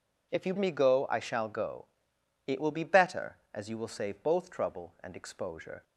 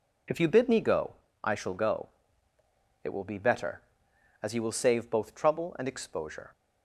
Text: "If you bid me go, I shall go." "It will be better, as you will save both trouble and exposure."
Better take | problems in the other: second | skips "bid"; at 0.5 s

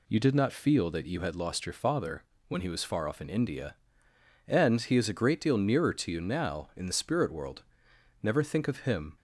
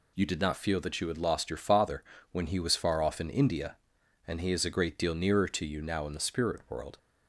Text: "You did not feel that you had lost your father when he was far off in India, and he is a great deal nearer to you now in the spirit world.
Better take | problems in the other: second | pauses between "father" and "when"; slight; at 2.2 s; 0.24 s long; slight in the second // goes on to say "Never think of him"; noticeable; from 8.2 s on; 0.94 s long

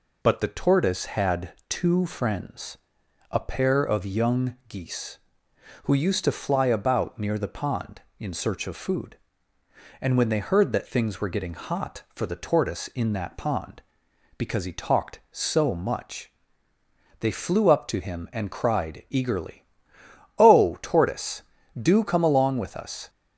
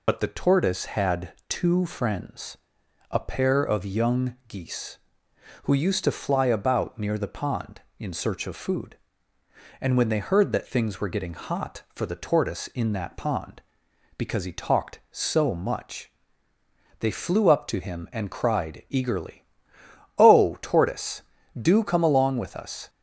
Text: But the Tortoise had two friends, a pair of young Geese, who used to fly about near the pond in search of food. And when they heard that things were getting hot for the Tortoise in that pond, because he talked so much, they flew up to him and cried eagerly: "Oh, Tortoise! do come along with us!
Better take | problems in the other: first | loses the start of "But"; at 0.0 s; 45 ms

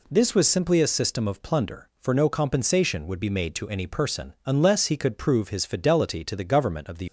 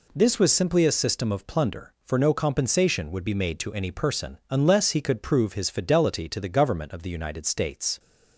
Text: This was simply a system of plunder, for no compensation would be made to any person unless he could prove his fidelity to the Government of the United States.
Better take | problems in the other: second | stops before "United States"; at 7.0 s

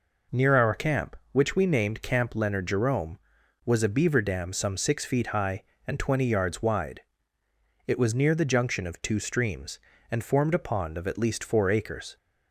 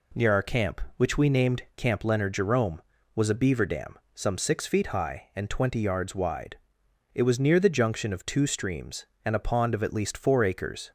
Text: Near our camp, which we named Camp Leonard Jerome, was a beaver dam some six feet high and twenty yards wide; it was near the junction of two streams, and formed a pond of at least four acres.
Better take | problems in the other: first | pauses between "dam" and "some"; slight; at 3.9 s; 0.16 s long // skips "formed"; at 9.3 s

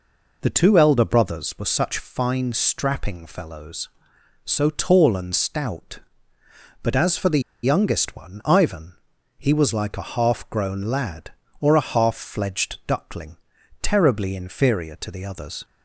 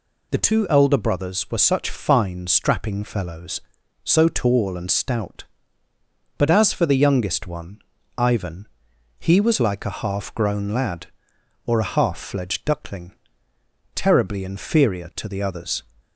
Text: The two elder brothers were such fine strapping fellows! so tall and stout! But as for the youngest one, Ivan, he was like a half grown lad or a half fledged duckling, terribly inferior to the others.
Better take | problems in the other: second | pauses between "the" and "youngest"; slight; at 7.3 s; 0.23 s long

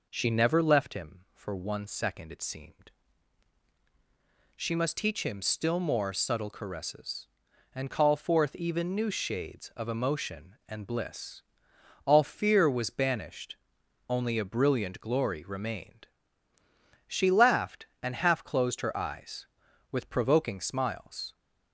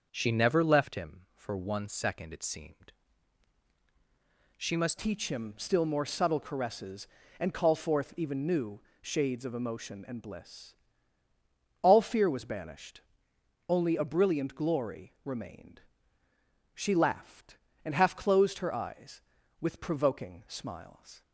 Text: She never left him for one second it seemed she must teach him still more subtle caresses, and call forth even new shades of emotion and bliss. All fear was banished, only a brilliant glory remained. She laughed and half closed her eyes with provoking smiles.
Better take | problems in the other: first | starts louder than the rest; noticeable; until 1.1 s; 6 dB // pauses between "seemed" and "she"; strong; at 2.9 s; 1.6 s long; strong in the first // changes voice at "teach"; from 4.9 s on; 16.3 s long // pauses between "new" and "shades"; slight; at 8.8 s; 0.18 s long

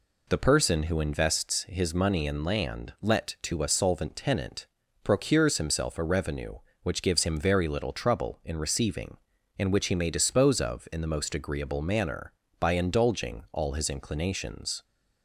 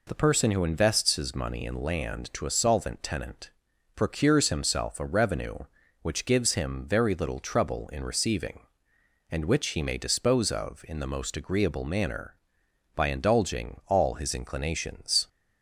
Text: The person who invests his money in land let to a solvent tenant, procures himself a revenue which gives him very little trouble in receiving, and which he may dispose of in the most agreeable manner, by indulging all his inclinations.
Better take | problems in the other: first | skips "let"; at 2.3 s

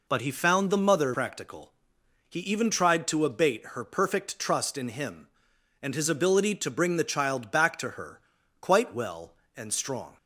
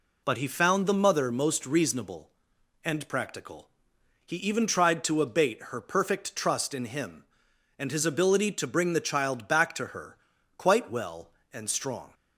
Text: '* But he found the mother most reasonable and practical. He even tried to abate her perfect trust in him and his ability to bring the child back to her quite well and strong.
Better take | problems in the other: second | skips "most reasonable and"; at 1.1 s // pauses between "her" and "quite"; at 8.1 s; 0.40 s long; also in the second

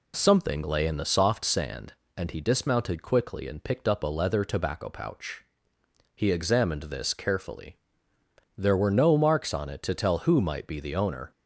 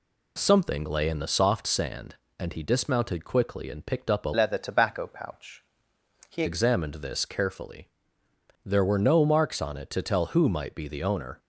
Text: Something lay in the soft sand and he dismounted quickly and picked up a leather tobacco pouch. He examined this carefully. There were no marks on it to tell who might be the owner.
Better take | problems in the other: first | changes voice from "leather" to "He"; from 4.3 to 6.4 s; 2.1 s long

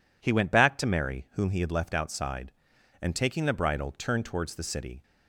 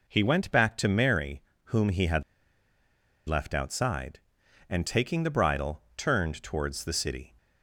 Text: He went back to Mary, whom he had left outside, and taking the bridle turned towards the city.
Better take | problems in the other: first | pauses between "had" and "left"; at 2.2 s; 1.0 s long // pauses between "bridle" and "turned"; slight; at 5.8 s; 0.16 s long

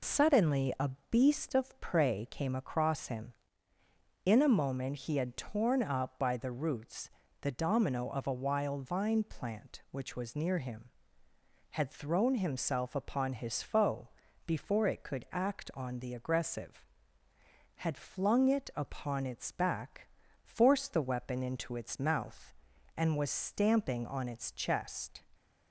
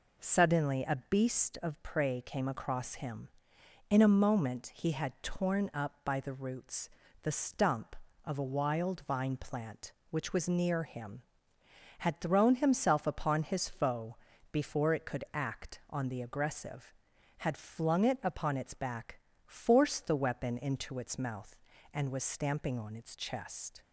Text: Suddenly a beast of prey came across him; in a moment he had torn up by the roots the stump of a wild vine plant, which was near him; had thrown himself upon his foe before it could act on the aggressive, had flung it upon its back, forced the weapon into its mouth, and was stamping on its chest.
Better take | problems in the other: second | pauses between "a" and "beast"; slight; at 0.8 s; 0.20 s long // pauses between "roots" and "the"; slight; at 7.0 s; 0.30 s long; slight in the second // says "domino" for "stump"; at 7.4 s // pauses between "foe" and "before"; slight; at 14.0 s; 0.36 s long; slight in the second

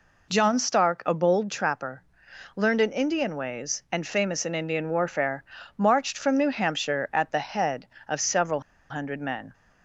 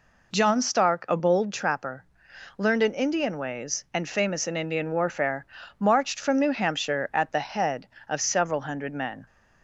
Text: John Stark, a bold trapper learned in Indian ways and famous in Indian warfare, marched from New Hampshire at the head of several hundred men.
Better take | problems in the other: second | pauses between "trapper" and "learned"; noticeable; at 2.0 s; 0.52 s long; noticeable in the second // pauses between "several" and "hundred"; slight; at 8.6 s; 0.29 s long

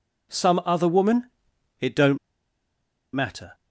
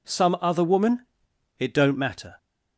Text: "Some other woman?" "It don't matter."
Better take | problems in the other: second | pauses between "don't" and "matter"; noticeable; at 2.1 s; 0.96 s long

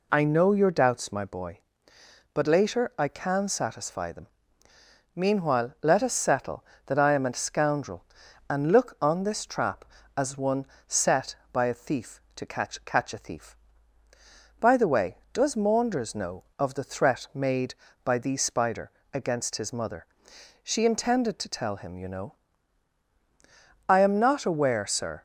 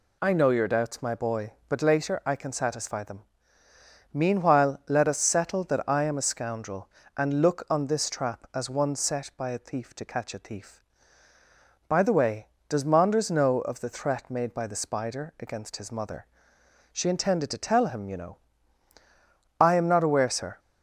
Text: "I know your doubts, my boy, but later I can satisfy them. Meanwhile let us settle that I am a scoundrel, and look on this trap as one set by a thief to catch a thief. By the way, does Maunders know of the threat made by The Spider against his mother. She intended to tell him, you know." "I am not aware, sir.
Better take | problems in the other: second | pauses between "one" and "set"; slight; at 10.6 s; 0.22 s long // says "catch" twice; at 12.8 s // pauses between "Spider" and "against"; slight; at 18.8 s; 0.24 s long

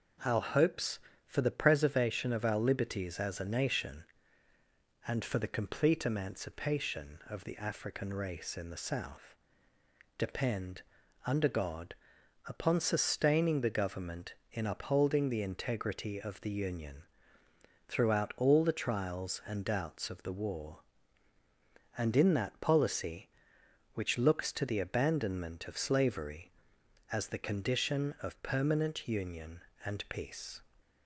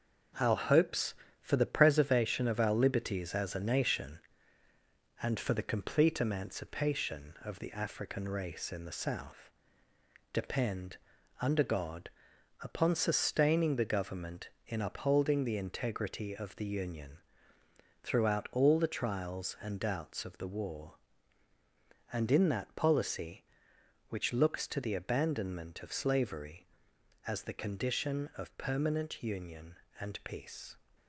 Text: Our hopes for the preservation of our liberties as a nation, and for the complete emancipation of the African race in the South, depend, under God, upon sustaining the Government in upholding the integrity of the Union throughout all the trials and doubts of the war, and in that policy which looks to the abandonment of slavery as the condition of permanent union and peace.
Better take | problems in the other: first | gets quieter; noticeable; throughout; 6 dB // pauses between "Union" and "throughout"; noticeable; at 17.1 s; 0.84 s long; noticeable in the first

